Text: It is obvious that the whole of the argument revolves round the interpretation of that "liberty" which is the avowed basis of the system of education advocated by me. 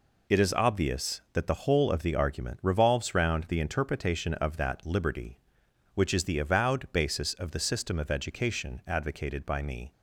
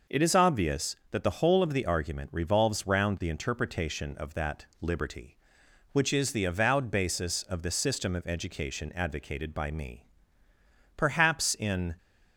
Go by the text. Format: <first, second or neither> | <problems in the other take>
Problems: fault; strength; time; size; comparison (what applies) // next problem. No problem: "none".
first | goes on to say "Perhaps in"; noticeable; from 10.9 s on; 0.98 s long